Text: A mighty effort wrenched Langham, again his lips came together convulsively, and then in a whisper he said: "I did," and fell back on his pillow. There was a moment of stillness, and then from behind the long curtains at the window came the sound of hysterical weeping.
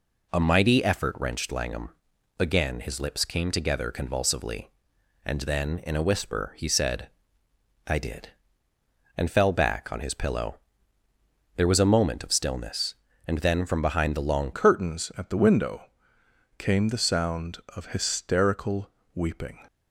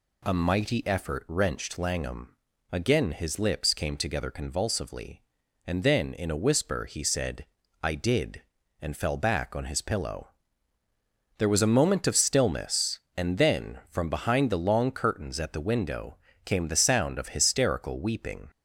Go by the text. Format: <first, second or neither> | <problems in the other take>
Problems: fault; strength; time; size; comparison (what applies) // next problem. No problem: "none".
second | changes voice at "curtains"; from 14.5 s on; 5.1 s long // pauses between "window" and "came"; noticeable; at 15.8 s; 0.74 s long; slight in the second // pauses between "hysterical" and "weeping"; slight; at 18.9 s; 0.24 s long